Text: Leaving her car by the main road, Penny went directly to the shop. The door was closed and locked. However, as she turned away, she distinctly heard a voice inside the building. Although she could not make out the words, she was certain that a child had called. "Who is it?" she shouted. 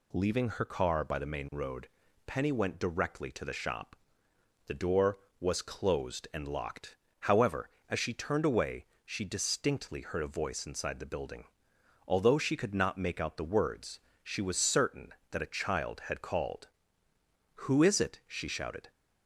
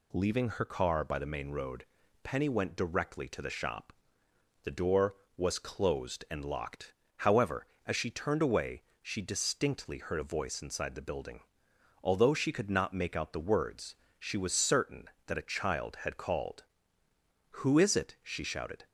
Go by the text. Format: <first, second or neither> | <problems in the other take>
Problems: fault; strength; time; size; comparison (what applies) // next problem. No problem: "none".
neither | none